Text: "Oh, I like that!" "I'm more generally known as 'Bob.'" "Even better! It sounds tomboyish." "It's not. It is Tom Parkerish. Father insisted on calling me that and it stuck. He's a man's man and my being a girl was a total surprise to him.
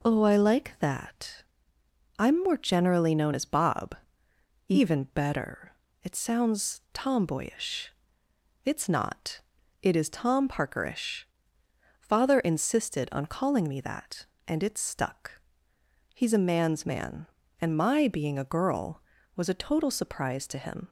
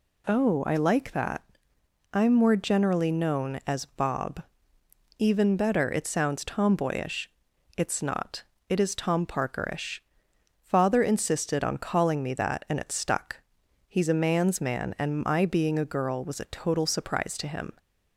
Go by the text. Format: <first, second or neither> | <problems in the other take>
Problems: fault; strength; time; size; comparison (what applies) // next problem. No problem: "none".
neither | none